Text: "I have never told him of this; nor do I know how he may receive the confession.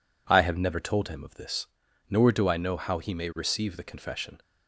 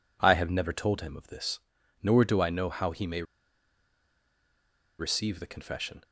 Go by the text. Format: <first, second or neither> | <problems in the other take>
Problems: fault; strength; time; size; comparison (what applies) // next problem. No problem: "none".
first | pauses between "may" and "receive"; strong; at 3.2 s; 1.7 s long